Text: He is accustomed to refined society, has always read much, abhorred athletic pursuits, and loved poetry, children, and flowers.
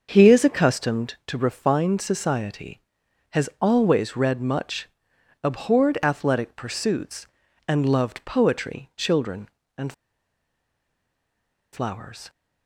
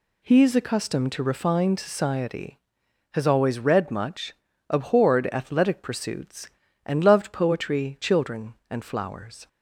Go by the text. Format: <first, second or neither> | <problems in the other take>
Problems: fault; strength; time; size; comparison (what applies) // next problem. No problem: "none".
second | starts louder than the rest; until 1.1 s; 6.5 dB // pauses between "and" and "flowers"; strong; at 9.9 s; 1.8 s long